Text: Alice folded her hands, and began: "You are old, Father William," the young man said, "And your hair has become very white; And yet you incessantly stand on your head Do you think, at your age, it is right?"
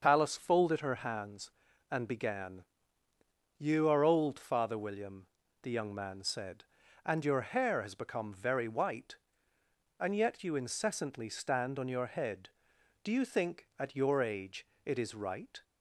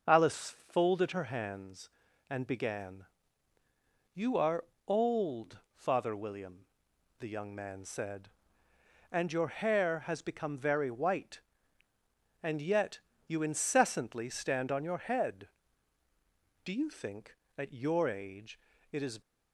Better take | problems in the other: first | starts louder than the rest; until 1.2 s; 6 dB; also in the first // pauses between "are" and "old"; slight; at 4.6 s; 0.22 s long // pauses between "yet" and "you"; slight; at 12.9 s; 0.28 s long // stops before "right"; at 19.2 s

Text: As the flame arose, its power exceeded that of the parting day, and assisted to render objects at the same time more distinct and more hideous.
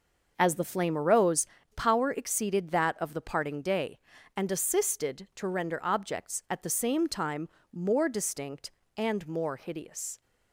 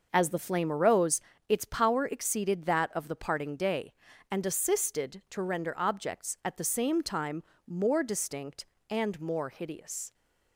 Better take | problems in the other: second | skips "its"; at 1.5 s // pauses between "time" and "more"; slight; at 7.4 s; 0.24 s long; slight in the second

